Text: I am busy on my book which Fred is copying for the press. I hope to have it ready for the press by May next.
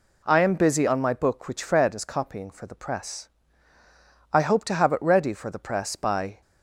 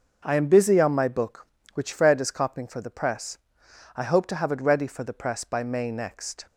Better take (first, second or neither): second